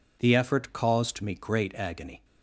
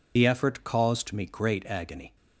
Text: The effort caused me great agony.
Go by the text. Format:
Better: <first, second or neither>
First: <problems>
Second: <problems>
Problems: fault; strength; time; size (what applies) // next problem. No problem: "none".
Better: first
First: none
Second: loses the start of "The"; at 0.1 s; 40 ms